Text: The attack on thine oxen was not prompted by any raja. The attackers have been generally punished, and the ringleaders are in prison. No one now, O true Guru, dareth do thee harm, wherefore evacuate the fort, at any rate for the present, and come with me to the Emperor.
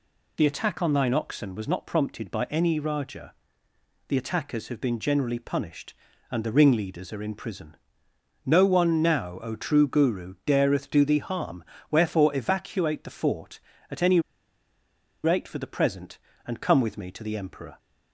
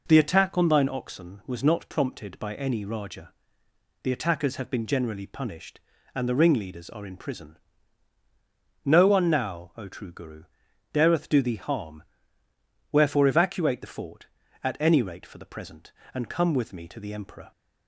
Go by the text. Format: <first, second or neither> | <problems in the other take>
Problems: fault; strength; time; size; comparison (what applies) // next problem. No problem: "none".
second | pauses between "any" and "rate"; at 14.2 s; 1.0 s long